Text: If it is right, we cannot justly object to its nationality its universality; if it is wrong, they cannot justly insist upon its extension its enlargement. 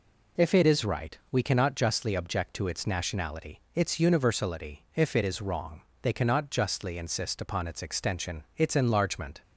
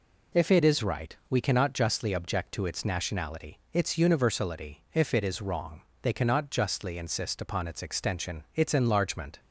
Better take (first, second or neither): neither